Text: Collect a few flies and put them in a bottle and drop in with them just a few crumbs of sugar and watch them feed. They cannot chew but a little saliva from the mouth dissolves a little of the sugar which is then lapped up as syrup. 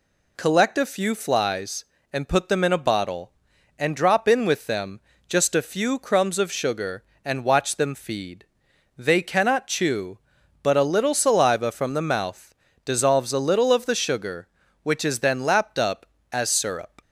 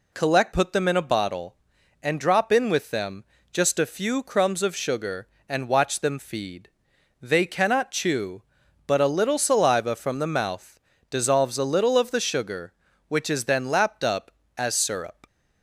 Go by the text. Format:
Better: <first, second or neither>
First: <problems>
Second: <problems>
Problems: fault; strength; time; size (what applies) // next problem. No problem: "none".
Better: first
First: pauses between "them" and "just"; slight; at 5.0 s; 0.28 s long // pauses between "mouth" and "dissolves"; slight; at 12.5 s; 0.30 s long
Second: skips "a few flies and"; at 0.5 s // pauses between "them" and "just"; slight; at 3.2 s; 0.28 s long // pauses between "mouth" and "dissolves"; slight; at 10.7 s; 0.30 s long